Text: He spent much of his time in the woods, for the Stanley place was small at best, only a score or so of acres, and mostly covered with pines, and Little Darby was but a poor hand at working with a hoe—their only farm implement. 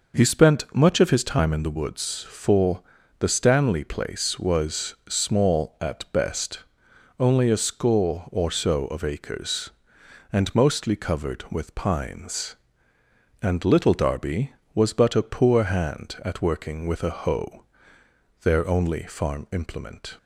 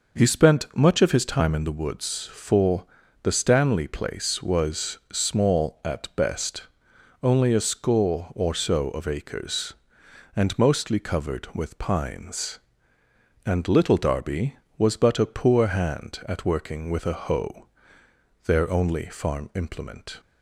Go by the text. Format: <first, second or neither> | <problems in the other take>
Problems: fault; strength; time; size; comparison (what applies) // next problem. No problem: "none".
neither | pauses between "for" and "the"; slight; the same in both // pauses between "was" and "small"; slight; the same in both